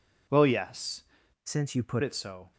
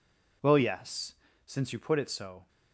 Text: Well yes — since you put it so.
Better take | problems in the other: second | changes voice from "since" to "put"; from 1.4 to 2.0 s; 0.6 s long

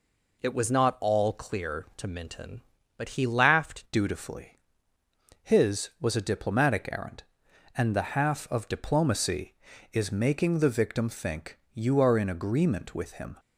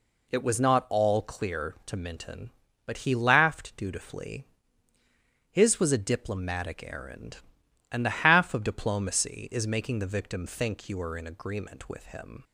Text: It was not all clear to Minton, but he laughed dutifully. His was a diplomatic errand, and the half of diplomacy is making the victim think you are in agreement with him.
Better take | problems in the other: second | changes voice at "dutifully"; from 3.9 s on; 9.4 s long // pauses between "think" and "you"; slight; at 11.5 s; 0.16 s long

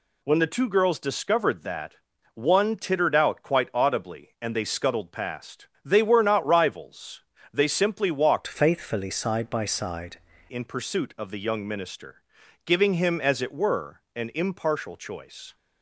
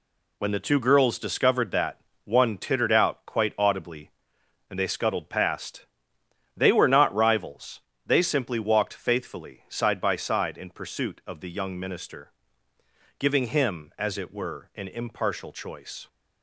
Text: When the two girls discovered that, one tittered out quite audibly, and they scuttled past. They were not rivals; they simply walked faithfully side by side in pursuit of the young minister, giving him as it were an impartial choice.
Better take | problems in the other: second | changes voice from "faithfully" to "side"; from 8.4 to 10.2 s; 1.8 s long

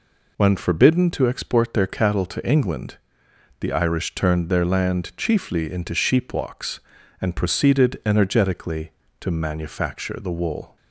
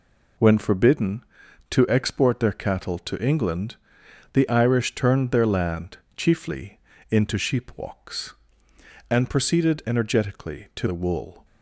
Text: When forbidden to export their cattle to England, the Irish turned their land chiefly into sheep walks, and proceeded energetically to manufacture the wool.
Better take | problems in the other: first | pauses between "land" and "chiefly"; slight; at 5.9 s; 0.18 s long // pauses between "chiefly" and "into"; slight; at 6.7 s; 0.30 s long // skips "manufacture"; at 10.8 s

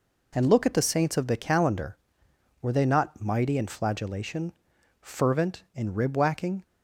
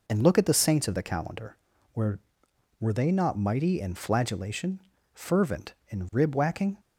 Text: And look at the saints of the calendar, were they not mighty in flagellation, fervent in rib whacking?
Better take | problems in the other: first | says "were" twice; at 2.7 s

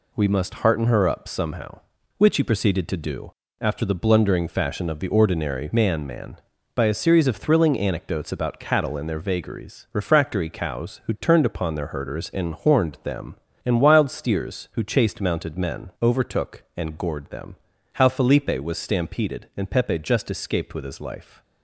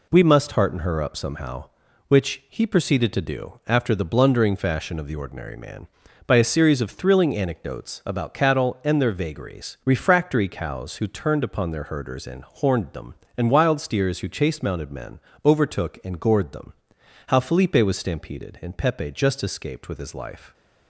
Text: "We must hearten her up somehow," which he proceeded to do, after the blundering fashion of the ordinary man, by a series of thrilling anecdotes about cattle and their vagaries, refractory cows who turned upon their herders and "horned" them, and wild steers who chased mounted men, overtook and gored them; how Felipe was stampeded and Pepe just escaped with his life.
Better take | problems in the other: second | says "man" twice; at 6.0 s

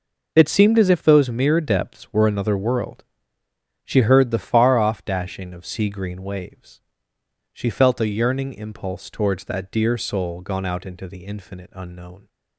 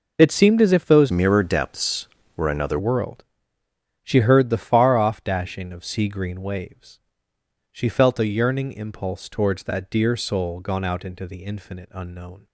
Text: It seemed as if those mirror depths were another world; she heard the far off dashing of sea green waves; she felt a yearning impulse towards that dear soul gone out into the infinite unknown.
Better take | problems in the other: first | changes voice from "mirror" to "another"; from 1.0 to 2.7 s; 1.7 s long

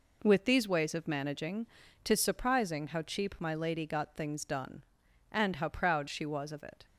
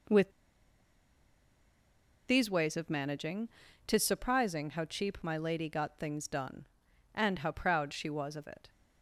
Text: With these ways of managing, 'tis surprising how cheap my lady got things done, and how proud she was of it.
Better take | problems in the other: first | pauses between "With" and "these"; strong; at 0.2 s; 1.9 s long

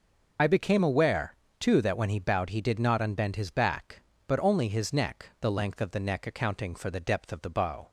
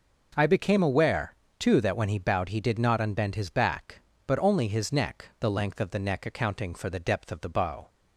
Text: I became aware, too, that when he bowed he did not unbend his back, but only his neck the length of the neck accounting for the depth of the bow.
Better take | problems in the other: second | loses the start of "I"; at 0.3 s; 65 ms

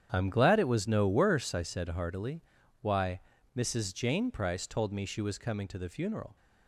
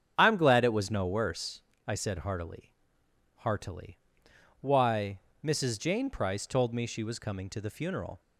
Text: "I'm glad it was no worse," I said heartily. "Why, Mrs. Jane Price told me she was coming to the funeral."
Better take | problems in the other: first | starts louder than the rest; strong; until 1.1 s; 8 dB; strong in the first // says "heartily" twice; at 3.3 s

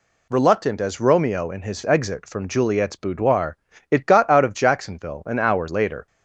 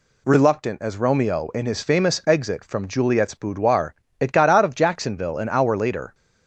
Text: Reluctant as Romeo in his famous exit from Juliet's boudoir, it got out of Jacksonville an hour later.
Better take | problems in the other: second | skips "famous"; at 1.8 s

